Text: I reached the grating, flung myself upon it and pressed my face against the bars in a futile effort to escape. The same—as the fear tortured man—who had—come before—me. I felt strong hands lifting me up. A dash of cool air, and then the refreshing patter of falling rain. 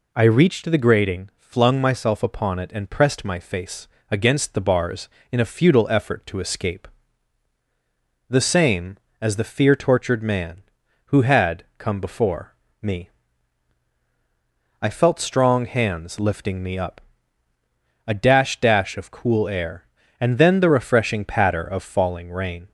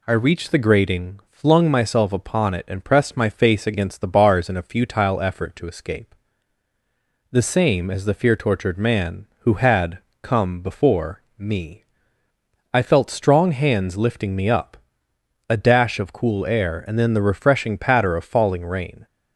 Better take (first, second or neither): second